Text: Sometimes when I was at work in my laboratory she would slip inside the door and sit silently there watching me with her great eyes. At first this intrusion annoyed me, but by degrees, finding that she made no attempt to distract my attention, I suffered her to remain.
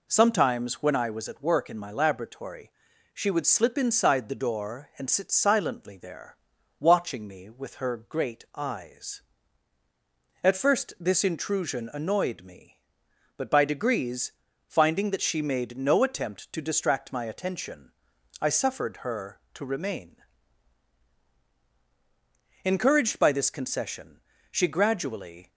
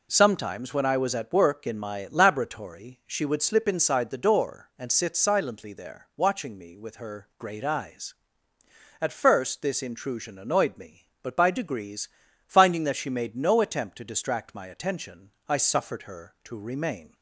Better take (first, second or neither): second